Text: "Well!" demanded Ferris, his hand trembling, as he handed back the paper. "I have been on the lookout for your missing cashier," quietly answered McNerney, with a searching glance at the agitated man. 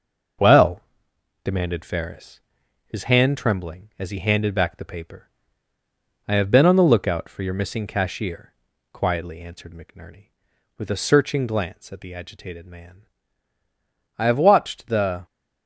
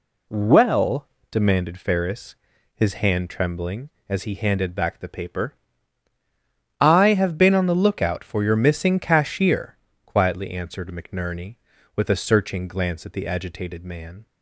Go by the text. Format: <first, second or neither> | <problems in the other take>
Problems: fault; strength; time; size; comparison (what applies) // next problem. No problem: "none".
second | starts louder than the rest; noticeable; until 2.0 s; 6 dB // goes on to say "I have watched the"; noticeable; from 14.1 s on; 1.1 s long